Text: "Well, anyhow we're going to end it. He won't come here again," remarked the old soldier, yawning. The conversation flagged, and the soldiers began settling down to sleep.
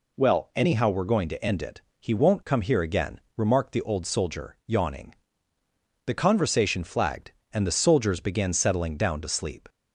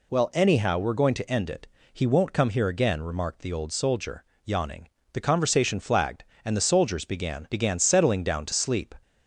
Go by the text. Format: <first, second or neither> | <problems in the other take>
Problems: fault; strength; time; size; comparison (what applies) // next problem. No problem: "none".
first | says "began" twice; at 7.5 s